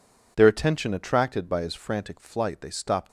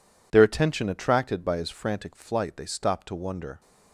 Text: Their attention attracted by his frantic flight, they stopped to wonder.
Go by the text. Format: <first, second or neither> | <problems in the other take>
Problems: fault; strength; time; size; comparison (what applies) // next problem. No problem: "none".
second | stops before "to wonder"; at 3.0 s